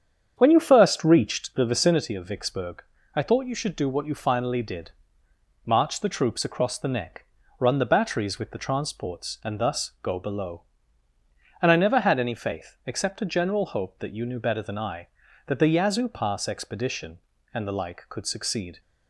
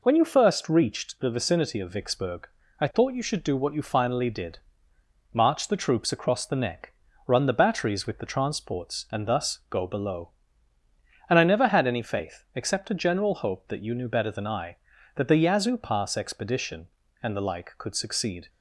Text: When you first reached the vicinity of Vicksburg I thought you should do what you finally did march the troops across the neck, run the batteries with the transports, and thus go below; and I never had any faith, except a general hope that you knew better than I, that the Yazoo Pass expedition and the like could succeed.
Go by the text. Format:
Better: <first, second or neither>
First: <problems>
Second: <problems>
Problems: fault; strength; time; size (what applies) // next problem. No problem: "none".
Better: second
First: starts louder than the rest; strong; until 2.1 s; 8 dB // pauses between "Vicksburg" and "I"; slight; at 2.8 s; 0.32 s long // pauses between "did" and "march"; noticeable; at 4.9 s; 0.74 s long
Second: pauses between "Vicksburg" and "I"; slight; at 2.4 s; 0.32 s long // pauses between "did" and "march"; noticeable; at 4.5 s; 0.74 s long